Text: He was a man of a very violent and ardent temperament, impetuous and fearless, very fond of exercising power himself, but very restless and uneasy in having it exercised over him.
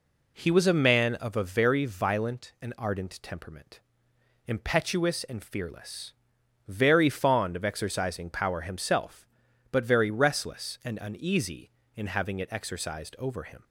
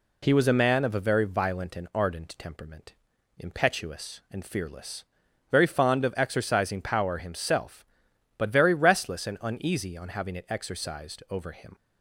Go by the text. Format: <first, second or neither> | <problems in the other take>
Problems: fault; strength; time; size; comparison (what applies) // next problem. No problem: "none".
first | says "on" for "in"; at 9.9 s